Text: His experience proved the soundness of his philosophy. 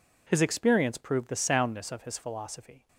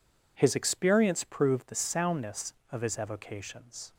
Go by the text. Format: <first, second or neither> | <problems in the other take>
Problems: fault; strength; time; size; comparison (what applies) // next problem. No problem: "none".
first | says "evocations" for "philosophy"; at 2.9 s